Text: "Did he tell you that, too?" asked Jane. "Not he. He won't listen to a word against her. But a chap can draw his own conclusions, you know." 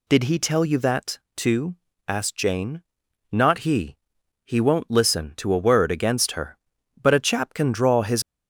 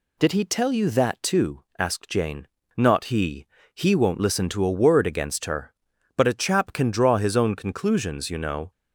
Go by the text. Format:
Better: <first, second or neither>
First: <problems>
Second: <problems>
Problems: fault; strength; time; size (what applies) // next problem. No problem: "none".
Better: second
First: stops before "own conclusions you know"; at 8.2 s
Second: none